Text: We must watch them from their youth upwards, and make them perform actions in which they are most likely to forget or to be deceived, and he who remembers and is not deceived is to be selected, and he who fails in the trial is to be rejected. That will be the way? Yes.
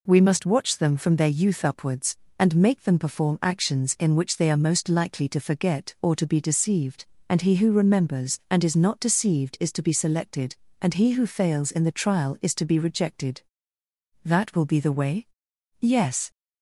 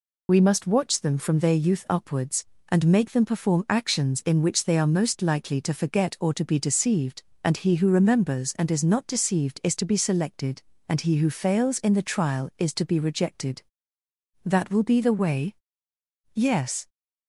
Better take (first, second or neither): first